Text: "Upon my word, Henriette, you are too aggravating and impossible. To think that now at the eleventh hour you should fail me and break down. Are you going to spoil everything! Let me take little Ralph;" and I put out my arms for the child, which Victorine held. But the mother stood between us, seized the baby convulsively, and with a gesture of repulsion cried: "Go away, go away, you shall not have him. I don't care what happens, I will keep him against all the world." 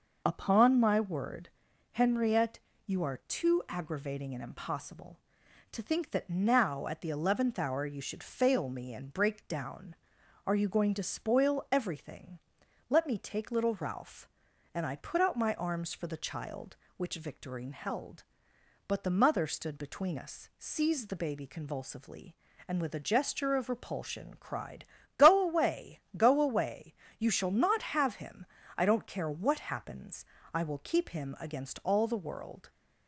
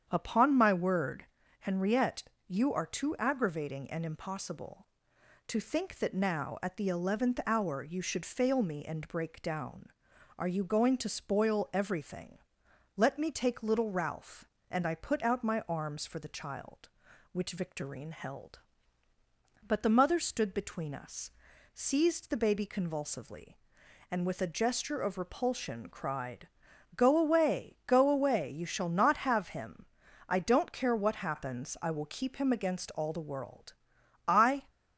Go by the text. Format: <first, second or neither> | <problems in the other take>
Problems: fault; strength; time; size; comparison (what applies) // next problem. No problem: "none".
first | starts louder than the rest; strong; until 1.1 s; 8.5 dB // goes on to say "I"; slight; from 34.2 s on; 0.40 s long